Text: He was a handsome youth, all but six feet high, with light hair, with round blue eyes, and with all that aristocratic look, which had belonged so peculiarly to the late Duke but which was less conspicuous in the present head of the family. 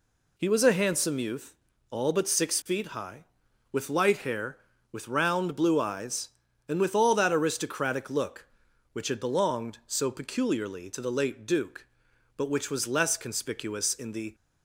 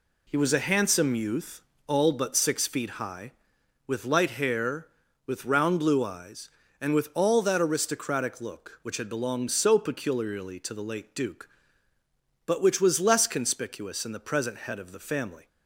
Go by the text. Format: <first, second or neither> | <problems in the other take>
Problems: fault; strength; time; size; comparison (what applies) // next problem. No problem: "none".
second | stops before "present head of the family"; at 14.3 s